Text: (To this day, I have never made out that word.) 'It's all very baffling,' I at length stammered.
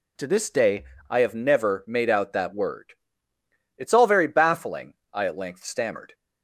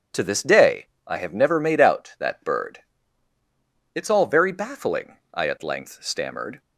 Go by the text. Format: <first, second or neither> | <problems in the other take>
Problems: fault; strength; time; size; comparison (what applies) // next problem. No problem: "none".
first | says "bird" for "word"; at 2.4 s